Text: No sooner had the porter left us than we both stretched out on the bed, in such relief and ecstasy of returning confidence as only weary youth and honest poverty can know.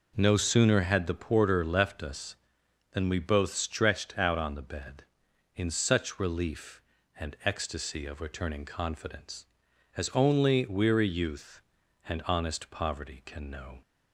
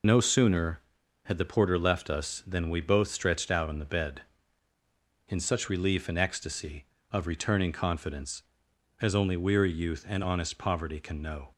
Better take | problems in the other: first | loses the start of "No"; at 0.0 s; 25 ms

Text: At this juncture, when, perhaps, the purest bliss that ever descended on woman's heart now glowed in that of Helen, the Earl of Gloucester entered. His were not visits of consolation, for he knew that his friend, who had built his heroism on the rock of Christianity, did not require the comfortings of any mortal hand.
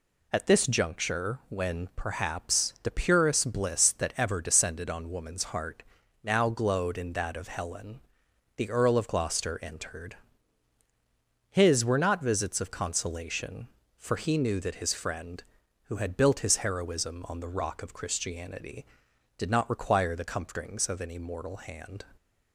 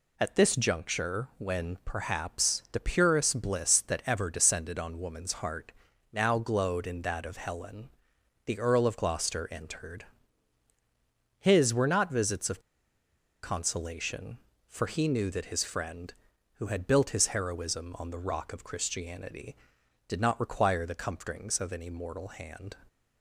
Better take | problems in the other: first | pauses between "heart" and "now"; at 5.7 s; 0.38 s long; also in the first // pauses between "of" and "consolation"; noticeable; at 12.5 s; 0.83 s long

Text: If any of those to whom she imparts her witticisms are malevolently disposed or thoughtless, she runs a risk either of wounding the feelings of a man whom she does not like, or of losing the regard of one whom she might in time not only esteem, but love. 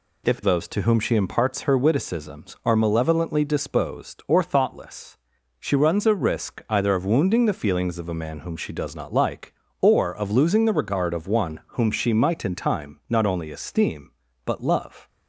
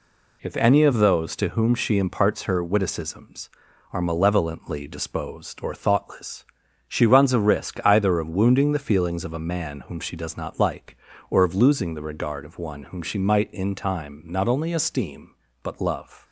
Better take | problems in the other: second | skips "any of"; at 0.4 s // pauses between "one" and "whom"; slight; at 11.5 s; 0.16 s long

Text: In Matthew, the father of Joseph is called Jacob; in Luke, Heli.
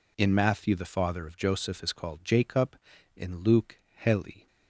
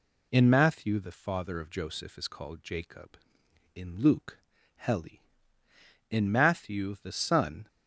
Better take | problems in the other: first | goes on to say "In Matthew the son"; from 6.0 s on; 1.5 s long

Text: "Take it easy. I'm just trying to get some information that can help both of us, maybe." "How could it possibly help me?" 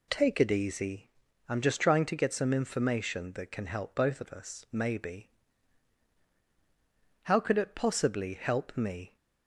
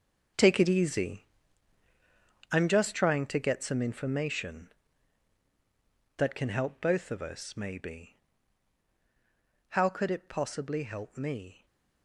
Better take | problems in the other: first | gets quieter; strong; throughout; 12 dB // stays silent after the last word; slight; from 11.5 s on; 0.5 s long

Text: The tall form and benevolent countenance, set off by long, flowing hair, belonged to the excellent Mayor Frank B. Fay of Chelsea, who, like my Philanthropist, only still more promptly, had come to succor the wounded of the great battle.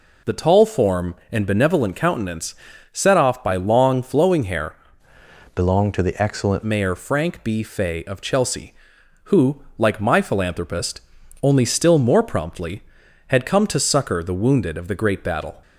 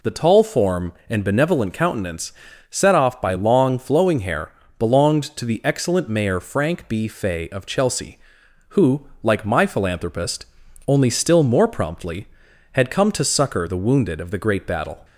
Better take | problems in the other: second | changes voice from "belonged" to "excellent"; from 5.5 to 6.6 s; 1.1 s long

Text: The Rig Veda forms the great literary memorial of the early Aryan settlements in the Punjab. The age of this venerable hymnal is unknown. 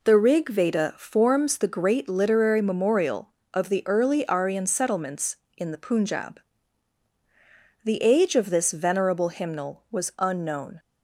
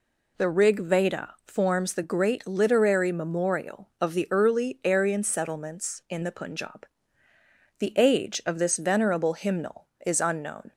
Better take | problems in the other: second | says "was" for "is"; at 9.9 s

